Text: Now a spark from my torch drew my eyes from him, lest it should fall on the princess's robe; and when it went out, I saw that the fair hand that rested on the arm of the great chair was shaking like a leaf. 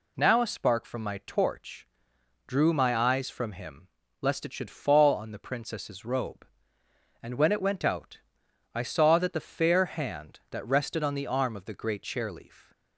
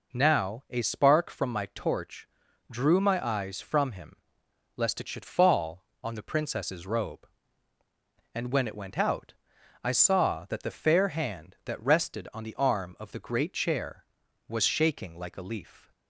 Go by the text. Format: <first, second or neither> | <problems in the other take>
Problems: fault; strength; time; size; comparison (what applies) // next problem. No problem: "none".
second | pauses between "torch" and "drew"; noticeable; at 1.8 s; 0.60 s long; also in the second // skips "was shaking like a"; at 12.3 s